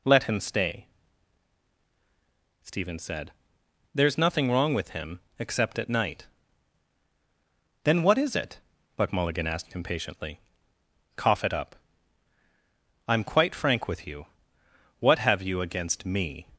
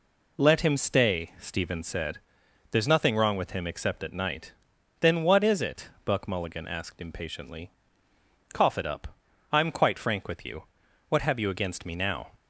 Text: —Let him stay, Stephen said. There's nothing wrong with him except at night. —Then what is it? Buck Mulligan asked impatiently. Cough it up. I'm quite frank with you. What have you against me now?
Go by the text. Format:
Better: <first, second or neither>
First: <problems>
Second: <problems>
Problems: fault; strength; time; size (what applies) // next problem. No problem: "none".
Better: second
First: pauses between "him" and "except"; slight; at 5.1 s; 0.20 s long // stops before "now"; at 16.5 s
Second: none